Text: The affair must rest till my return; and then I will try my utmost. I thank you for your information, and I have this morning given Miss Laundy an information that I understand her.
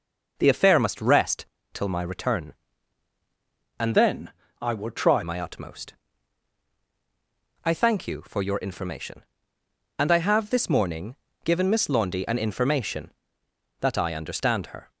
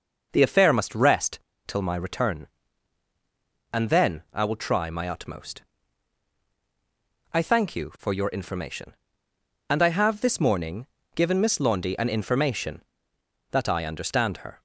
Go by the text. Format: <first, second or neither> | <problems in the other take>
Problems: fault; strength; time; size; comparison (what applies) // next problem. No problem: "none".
second | pauses between "rest" and "till"; slight; at 1.4 s; 0.26 s long; slight in the second // changes voice from "then" to "try"; from 3.9 to 5.2 s; 1.3 s long // pauses between "then" and "I"; slight; at 4.3 s; 0.28 s long // pauses between "morning" and "given"; slight; at 11.1 s; 0.28 s long; slight in the second